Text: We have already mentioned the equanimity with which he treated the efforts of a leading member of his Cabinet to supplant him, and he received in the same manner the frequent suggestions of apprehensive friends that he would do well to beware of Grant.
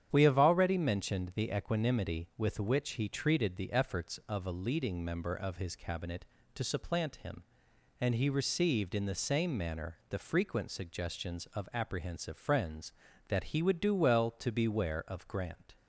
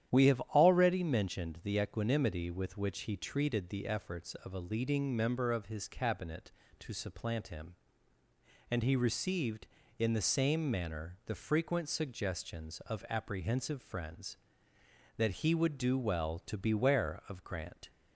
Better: neither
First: starts louder than the rest; strong; until 1.1 s; 9 dB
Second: starts louder than the rest; strong; until 1.1 s; 10.5 dB

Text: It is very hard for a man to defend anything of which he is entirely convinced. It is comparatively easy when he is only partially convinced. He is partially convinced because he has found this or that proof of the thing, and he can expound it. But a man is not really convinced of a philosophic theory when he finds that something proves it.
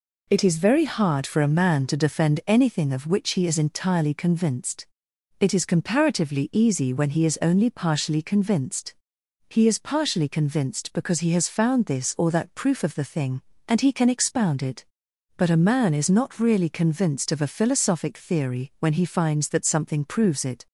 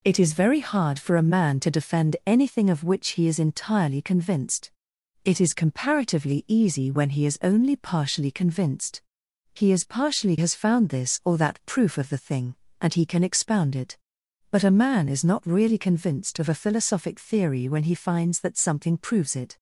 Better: first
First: none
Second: skips "convinced because he"; at 10.3 s

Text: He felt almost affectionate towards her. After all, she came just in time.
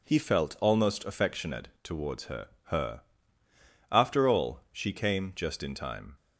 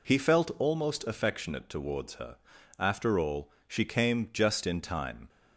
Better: second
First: says "her" twice; at 2.6 s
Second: none

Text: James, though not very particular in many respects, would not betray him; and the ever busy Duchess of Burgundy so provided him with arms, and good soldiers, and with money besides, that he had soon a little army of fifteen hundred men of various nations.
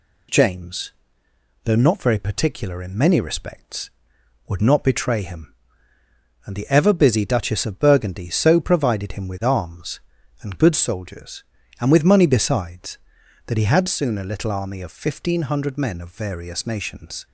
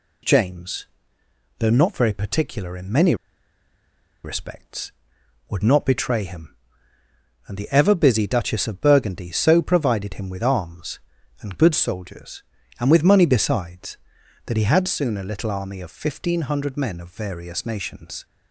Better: first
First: none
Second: pauses between "many" and "respects"; at 3.1 s; 1.1 s long

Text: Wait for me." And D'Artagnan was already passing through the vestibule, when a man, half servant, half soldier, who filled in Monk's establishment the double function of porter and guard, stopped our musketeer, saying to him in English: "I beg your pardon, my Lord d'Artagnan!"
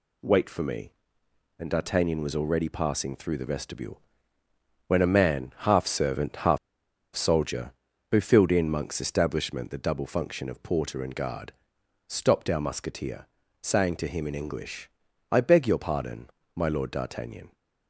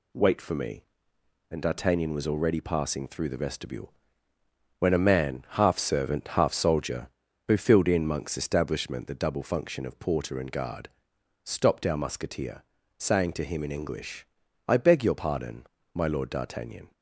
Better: second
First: pauses between "half" and "soldier"; noticeable; at 6.5 s; 0.57 s long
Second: none

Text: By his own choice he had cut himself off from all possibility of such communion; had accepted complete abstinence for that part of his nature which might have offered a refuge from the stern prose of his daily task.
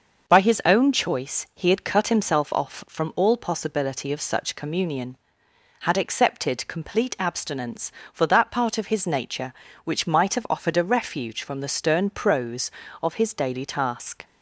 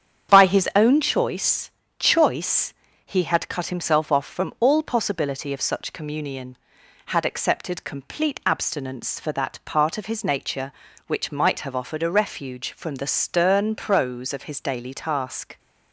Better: first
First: none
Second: starts louder than the rest; strong; until 1.3 s; 8.5 dB // says "choice" twice; at 1.9 s

